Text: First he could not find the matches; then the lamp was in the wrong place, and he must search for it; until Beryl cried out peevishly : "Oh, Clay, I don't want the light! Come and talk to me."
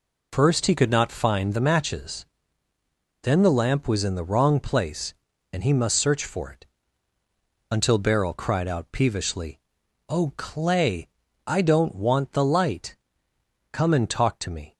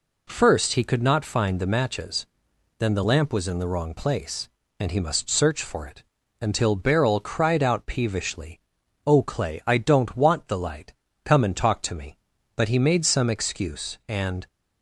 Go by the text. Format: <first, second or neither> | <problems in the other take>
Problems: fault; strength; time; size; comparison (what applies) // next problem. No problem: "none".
first | goes on to say "But he made some excuse and"; strong; from 12.5 s on; 1.9 s long